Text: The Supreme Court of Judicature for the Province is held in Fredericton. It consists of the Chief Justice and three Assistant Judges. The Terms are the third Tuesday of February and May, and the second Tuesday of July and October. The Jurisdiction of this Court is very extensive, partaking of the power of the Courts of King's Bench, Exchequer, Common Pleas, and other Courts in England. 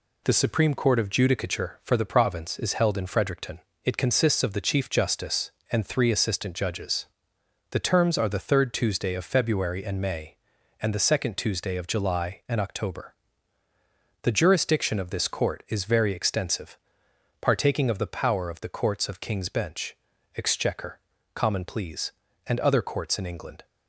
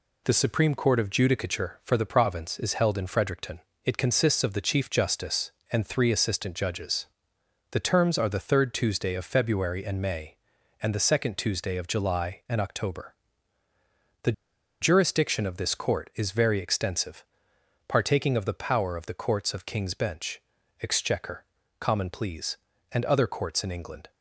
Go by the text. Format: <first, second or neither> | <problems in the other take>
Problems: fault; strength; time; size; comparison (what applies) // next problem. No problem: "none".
first | pauses between "The" and "Jurisdiction"; noticeable; at 14.3 s; 0.49 s long